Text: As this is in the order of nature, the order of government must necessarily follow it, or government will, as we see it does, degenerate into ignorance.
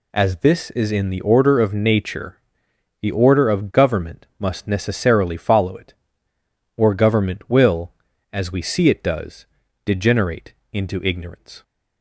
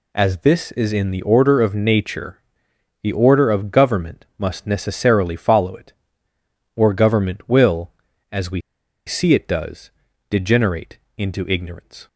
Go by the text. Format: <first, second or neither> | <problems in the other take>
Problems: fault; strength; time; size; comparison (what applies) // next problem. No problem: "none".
first | pauses between "we" and "see"; noticeable; at 8.5 s; 0.47 s long // pauses between "degenerate" and "into"; slight; at 10.9 s; 0.20 s long; slight in the first